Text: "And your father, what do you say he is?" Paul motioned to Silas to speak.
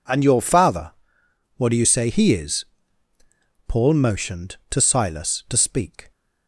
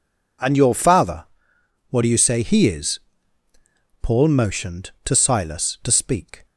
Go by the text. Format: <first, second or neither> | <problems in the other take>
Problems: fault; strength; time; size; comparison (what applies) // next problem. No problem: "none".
neither | none